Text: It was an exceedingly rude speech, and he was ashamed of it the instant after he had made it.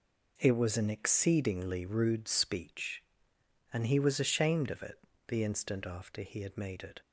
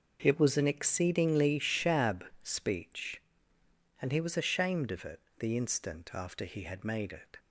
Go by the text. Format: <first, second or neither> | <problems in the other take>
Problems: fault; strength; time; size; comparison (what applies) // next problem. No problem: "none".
first | starts louder than the rest; noticeable; until 1.2 s; 6 dB // says "shab" for "rude"; at 1.5 s // pauses between "it" and "the"; slight; at 5.1 s; 0.20 s long; slight in the first